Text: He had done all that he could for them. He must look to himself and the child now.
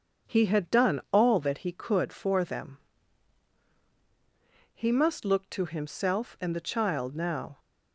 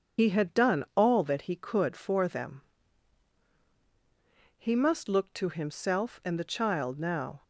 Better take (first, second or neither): first